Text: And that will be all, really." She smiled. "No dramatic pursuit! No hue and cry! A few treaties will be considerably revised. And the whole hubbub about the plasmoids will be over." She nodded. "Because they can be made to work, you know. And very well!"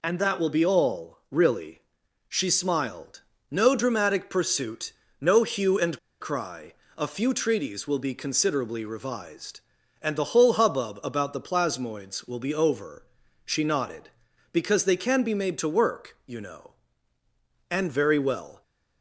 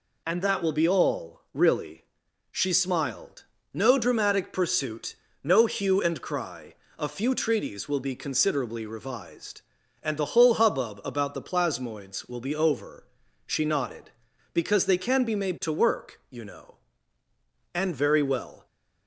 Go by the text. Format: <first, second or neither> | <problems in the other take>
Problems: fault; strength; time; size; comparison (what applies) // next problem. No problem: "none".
second | pauses between "and" and "cry"; slight; at 5.9 s; 0.22 s long